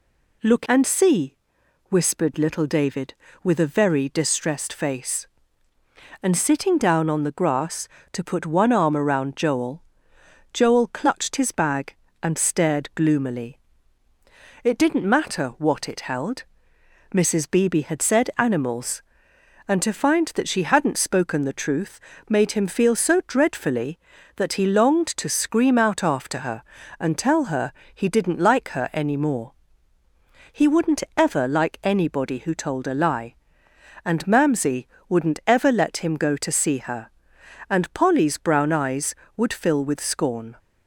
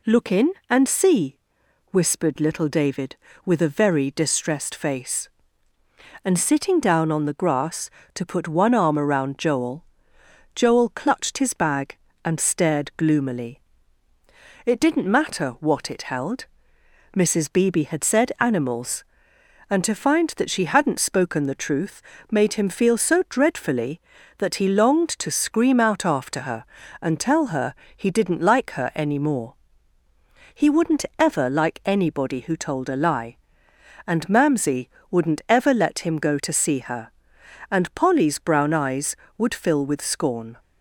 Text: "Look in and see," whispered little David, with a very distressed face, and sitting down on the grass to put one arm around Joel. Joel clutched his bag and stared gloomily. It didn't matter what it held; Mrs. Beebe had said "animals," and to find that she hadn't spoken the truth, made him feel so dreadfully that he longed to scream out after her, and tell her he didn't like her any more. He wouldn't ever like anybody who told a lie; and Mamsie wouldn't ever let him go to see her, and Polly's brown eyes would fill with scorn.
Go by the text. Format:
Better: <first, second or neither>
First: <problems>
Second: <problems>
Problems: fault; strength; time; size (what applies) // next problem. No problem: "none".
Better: second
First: skips "in"; at 0.6 s // pauses between "her" and "he"; slight; at 27.7 s; 0.24 s long // pauses between "Mamsie" and "wouldn't"; slight; at 34.8 s; 0.20 s long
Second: pauses between "her" and "he"; slight; at 27.7 s; 0.24 s long // pauses between "Mamsie" and "wouldn't"; slight; at 34.9 s; 0.20 s long